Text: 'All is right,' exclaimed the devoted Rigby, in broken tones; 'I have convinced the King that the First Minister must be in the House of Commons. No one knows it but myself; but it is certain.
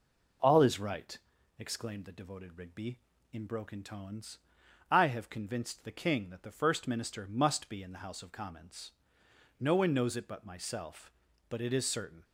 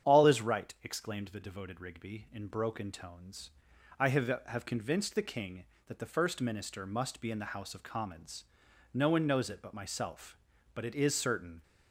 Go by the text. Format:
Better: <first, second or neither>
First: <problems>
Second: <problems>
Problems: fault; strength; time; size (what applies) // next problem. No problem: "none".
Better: first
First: none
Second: starts louder than the rest; strong; until 1.1 s; 8.5 dB // says "have" twice; at 4.4 s